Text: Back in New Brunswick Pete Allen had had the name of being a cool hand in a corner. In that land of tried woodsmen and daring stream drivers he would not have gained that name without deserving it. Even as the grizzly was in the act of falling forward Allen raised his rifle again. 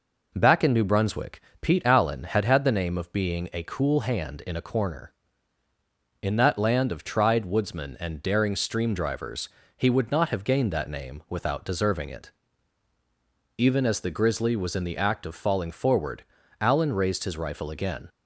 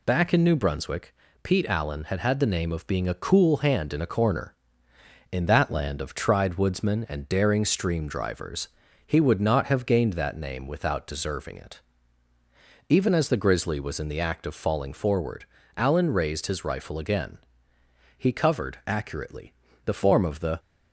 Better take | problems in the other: first | pauses between "Brunswick" and "Pete"; slight; at 1.1 s; 0.28 s long; slight in the first // pauses between "drivers" and "he"; at 8.6 s; 0.38 s long; slight in the first // pauses between "forward" and "Allen"; slight; at 15.4 s; 0.32 s long; also in the first // goes on to say "He covered accurately the form of the"; strong; from 18.1 s on; 2.4 s long

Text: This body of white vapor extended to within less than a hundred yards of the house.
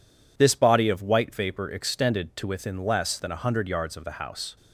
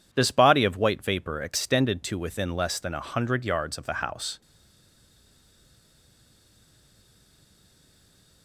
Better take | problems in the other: first | stays silent after the last word; strong; from 4.4 s on; 4.0 s long

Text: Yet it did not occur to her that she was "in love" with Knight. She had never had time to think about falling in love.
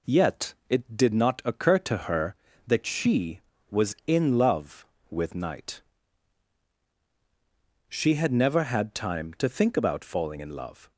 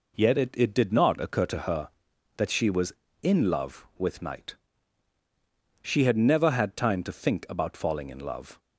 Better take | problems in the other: first | says "it" twice; at 0.5 s

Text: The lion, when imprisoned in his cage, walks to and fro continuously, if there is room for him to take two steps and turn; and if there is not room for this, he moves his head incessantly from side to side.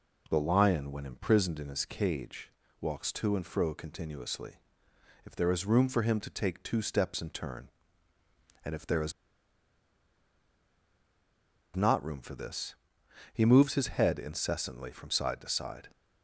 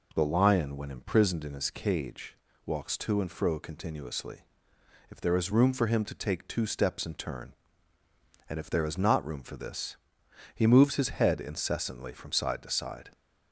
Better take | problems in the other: second | pauses between "is" and "not"; strong; at 9.1 s; 2.6 s long

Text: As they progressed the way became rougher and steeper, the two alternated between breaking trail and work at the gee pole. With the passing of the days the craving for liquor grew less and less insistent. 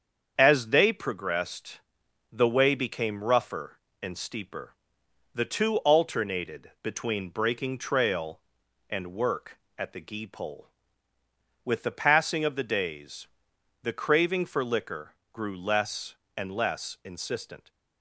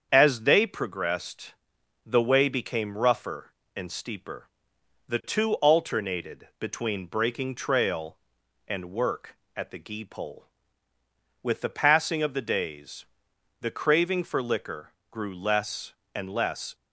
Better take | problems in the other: first | starts louder than the rest; strong; until 1.1 s; 7.5 dB; strong in the first // pauses between "progressed" and "the"; noticeable; at 1.5 s; 0.52 s long; noticeable in the first // pauses between "days" and "the"; noticeable; at 13.0 s; 0.56 s long; noticeable in the first // pauses between "liquor" and "grew"; slight; at 14.9 s; 0.18 s long; slight in the first // stops before "insistent"; at 16.7 s

